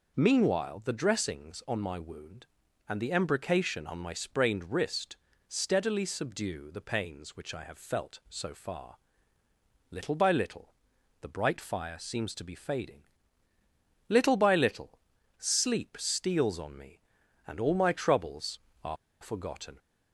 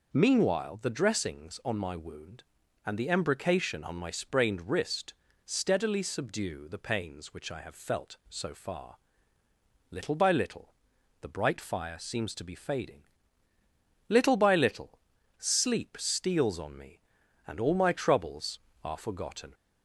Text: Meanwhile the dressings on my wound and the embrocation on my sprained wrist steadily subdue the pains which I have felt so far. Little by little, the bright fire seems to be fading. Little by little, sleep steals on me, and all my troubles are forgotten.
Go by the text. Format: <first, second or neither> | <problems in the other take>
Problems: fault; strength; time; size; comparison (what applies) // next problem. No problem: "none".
second | pauses between "wrist" and "steadily"; slight; at 5.1 s; 0.32 s long; slight in the second // pauses between "are" and "forgotten"; slight; at 18.9 s; 0.25 s long